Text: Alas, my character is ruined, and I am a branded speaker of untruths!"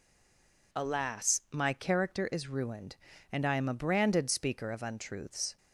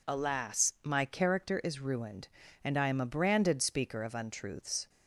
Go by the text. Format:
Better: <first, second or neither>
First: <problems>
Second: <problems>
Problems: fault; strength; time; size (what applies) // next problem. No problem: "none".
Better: second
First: stays silent before the first word; slight; until 0.7 s; 0.7 s long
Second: none